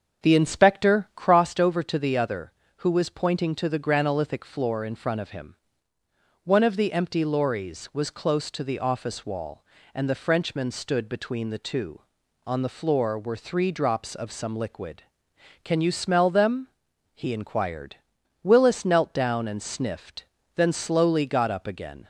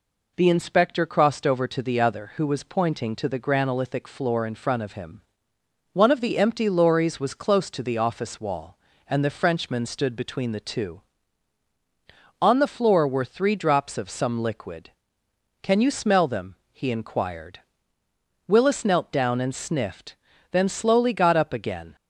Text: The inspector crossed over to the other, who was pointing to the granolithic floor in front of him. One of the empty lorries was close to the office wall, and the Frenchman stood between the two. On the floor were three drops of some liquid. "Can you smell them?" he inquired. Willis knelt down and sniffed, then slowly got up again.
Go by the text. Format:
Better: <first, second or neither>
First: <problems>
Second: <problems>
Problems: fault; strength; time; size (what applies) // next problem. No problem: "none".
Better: second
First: starts louder than the rest; until 1.4 s; 7 dB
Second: none